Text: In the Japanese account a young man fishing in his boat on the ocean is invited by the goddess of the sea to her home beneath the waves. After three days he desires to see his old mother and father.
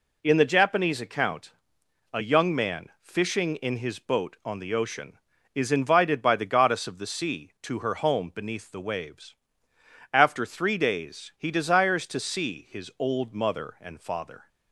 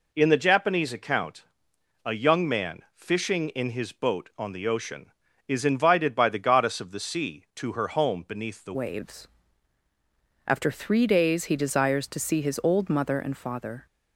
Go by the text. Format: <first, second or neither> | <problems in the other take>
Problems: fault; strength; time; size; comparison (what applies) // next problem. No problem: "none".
first | pauses between "account" and "a"; noticeable; at 1.4 s; 0.60 s long; noticeable in the first // changes voice at "waves"; from 8.7 s on; 5.1 s long